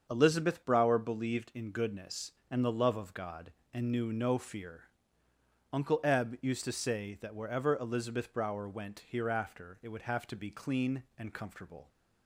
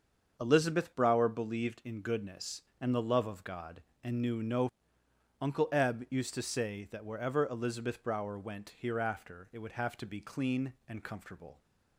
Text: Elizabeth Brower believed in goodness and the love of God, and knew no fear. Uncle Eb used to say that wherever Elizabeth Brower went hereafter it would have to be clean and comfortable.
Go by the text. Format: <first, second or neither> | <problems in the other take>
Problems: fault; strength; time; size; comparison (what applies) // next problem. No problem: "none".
first | starts louder than the rest; until 1.4 s; 7 dB; also in the first // skips "fear"; at 5.0 s